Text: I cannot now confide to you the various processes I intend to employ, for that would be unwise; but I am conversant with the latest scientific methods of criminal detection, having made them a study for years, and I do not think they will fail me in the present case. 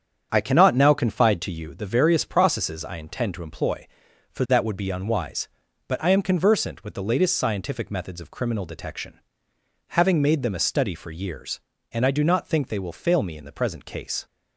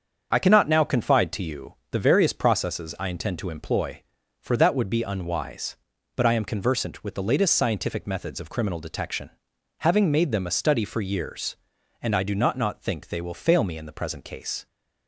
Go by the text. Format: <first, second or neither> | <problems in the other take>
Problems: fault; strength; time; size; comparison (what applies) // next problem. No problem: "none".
first | starts louder than the rest; until 1.3 s; 7 dB; strong in the first // pauses between "you" and "the"; slight; at 1.7 s; 0.18 s long // says "not" twice; at 12.5 s